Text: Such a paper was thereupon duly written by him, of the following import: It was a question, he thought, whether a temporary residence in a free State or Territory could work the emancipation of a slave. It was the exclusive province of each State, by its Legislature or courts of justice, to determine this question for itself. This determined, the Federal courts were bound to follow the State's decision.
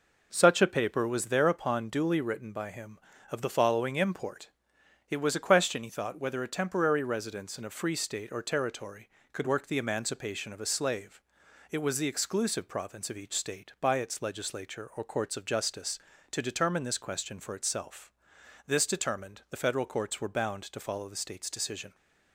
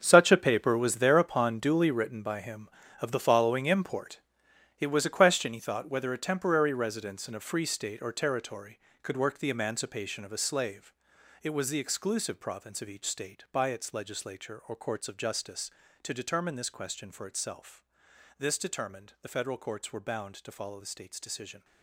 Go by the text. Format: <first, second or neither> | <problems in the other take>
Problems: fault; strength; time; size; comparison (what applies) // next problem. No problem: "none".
first | gets quieter; strong; throughout; 13.5 dB